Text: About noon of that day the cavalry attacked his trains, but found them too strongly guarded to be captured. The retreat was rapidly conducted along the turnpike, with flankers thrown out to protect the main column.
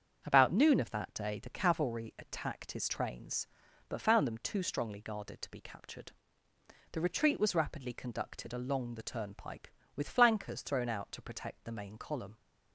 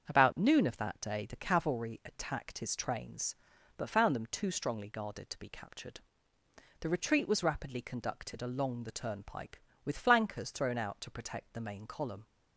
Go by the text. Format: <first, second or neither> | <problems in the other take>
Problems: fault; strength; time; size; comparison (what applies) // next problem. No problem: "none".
neither | starts louder than the rest; strong; the same in both